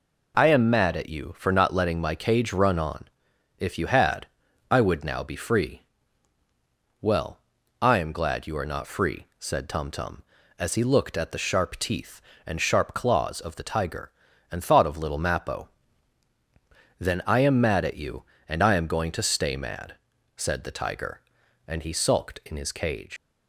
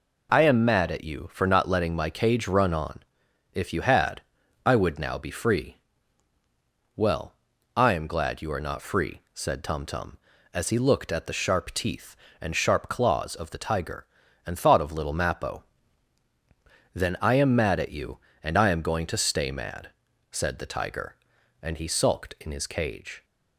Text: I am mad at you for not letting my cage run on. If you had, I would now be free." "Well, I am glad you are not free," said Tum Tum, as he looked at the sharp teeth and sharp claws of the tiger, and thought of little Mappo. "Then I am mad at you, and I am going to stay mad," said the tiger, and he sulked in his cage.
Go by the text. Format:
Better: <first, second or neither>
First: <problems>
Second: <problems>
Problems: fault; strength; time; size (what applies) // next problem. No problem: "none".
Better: second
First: leaves "cage" unfinished; at 23.1 s; 135 ms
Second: none